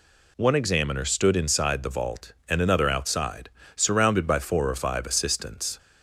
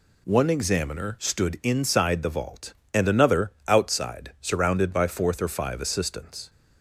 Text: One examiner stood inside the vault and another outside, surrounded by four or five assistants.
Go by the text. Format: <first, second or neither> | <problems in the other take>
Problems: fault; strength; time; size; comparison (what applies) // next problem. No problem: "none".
first | pauses between "another" and "outside"; slight; at 3.5 s; 0.16 s long // says "fourth" for "four"; at 5.0 s